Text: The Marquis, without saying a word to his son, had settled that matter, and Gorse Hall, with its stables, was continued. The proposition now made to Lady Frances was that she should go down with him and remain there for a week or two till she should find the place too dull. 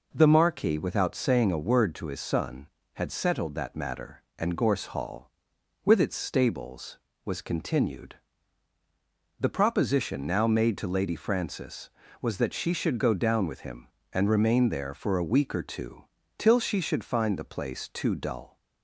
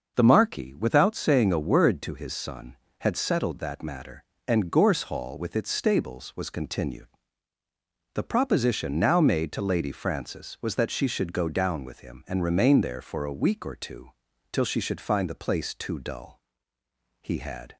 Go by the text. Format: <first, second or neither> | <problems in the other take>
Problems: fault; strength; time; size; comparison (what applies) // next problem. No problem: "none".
first | starts louder than the rest; until 1.1 s; 6 dB // pauses between "two" and "till"; at 14.1 s; 0.40 s long; slight in the first // goes on to say "He had"; from 17.2 s on; 0.54 s long